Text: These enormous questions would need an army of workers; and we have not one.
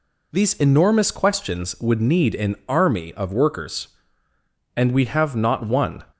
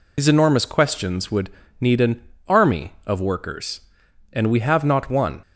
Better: first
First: none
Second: loses the start of "These"; at 0.1 s; 45 ms // pauses between "would" and "need"; slight; at 1.4 s; 0.30 s long // pauses between "an" and "army"; slight; at 2.2 s; 0.24 s long

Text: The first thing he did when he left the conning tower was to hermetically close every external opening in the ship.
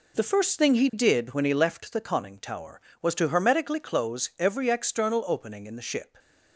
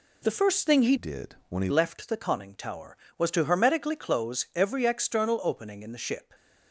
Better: first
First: none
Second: changes voice from "did" to "he"; from 0.9 to 1.7 s; 0.8 s long

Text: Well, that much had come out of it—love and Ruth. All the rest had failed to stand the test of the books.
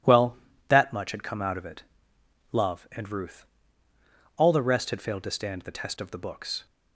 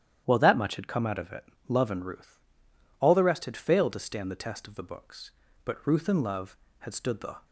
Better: first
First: none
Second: starts louder than the rest; strong; until 1.2 s; 10.5 dB // goes on to say "But Ruth and love had stood the"; strong; from 5.6 s on; 1.8 s long

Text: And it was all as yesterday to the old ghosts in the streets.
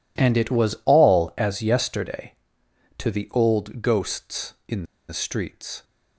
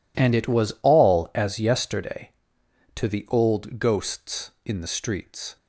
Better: second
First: pauses between "in" and "the"; slight; at 4.8 s; 0.25 s long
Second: none

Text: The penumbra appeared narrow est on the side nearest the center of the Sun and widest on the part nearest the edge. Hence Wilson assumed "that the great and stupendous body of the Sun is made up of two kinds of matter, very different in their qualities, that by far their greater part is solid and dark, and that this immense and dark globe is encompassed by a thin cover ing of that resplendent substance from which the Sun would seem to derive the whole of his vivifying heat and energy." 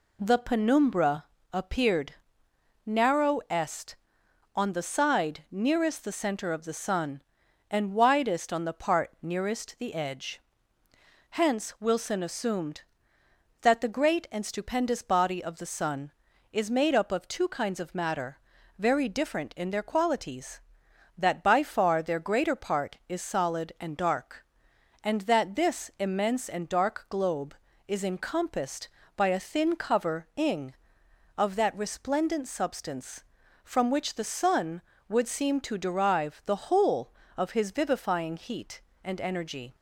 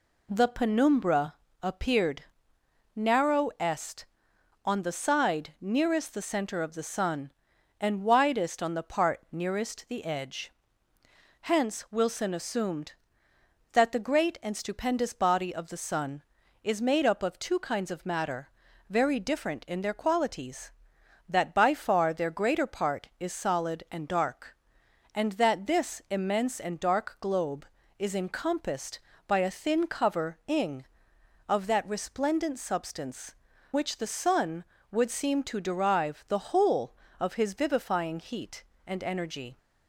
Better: first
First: pauses between "penumbra" and "appeared"; slight; at 1.2 s; 0.26 s long // pauses between "appeared" and "narrow"; noticeable; at 2.1 s; 0.72 s long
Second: pauses between "penumbra" and "appeared"; slight; at 1.3 s; 0.26 s long // pauses between "appeared" and "narrow"; noticeable; at 2.2 s; 0.72 s long // skips "from"; at 33.5 s

